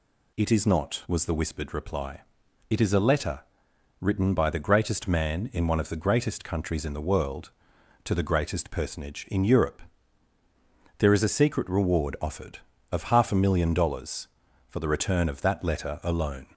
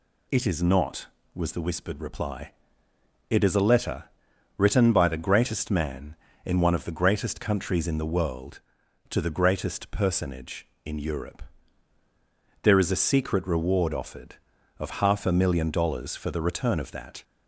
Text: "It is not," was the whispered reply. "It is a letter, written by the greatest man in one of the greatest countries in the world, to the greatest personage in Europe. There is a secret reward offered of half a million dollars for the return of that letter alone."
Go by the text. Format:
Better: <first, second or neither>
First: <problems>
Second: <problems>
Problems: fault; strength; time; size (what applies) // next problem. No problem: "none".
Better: first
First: none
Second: stops before "letter alone"; at 17.2 s